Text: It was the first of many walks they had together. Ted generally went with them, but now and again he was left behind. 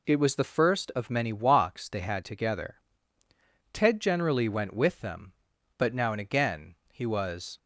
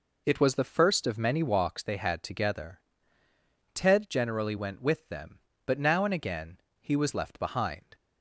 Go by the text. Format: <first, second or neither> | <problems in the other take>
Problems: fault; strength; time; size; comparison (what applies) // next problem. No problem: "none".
second | pauses between "again" and "he"; slight; at 6.7 s; 0.16 s long; slight in the second // stops before "left behind"; at 7.5 s